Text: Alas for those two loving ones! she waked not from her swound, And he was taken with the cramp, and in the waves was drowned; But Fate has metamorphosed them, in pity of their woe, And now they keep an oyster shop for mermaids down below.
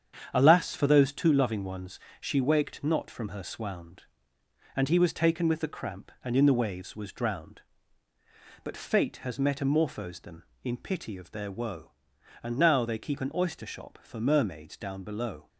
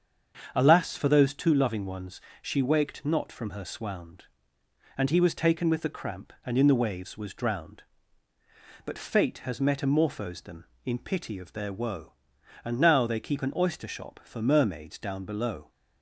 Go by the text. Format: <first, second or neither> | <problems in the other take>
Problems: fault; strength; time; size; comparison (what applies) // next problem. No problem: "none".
second | gets quieter; throughout; 6.5 dB // starts louder than the rest; strong; until 1.3 s; 8 dB; strong in the second